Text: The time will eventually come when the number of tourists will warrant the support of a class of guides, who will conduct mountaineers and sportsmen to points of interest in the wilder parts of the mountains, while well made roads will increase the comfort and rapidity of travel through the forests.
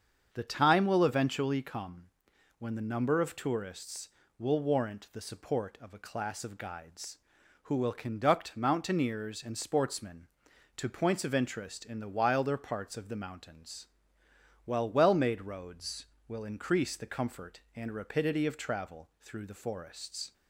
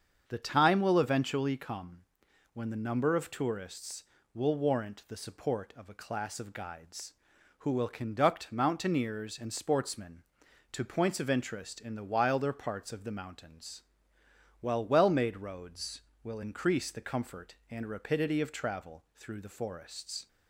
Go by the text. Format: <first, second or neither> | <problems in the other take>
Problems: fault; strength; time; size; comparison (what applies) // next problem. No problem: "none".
neither | starts louder than the rest; strong; the same in both // pauses between "come" and "when"; noticeable; the same in both